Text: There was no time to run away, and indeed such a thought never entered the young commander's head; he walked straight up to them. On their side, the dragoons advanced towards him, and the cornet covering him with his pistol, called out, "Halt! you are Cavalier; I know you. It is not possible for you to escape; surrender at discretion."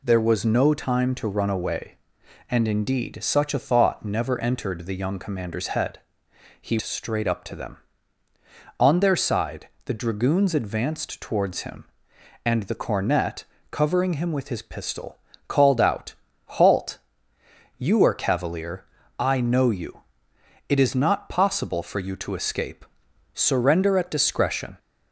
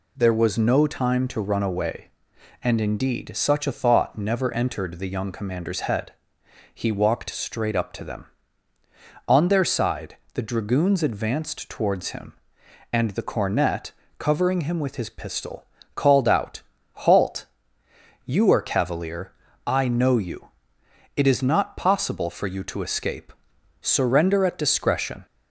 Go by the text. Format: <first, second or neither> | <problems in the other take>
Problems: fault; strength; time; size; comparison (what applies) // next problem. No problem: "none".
second | skips "walked"; at 6.7 s // pauses between "cornet" and "covering"; slight; at 13.4 s; 0.26 s long; slight in the second